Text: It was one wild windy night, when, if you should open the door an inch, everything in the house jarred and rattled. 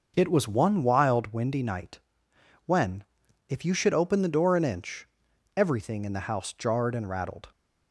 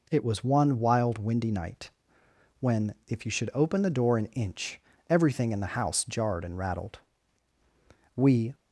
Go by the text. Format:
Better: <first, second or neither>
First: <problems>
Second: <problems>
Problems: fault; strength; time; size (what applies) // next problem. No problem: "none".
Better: first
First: none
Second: goes on to say "We"; slight; from 8.1 s on; 0.38 s long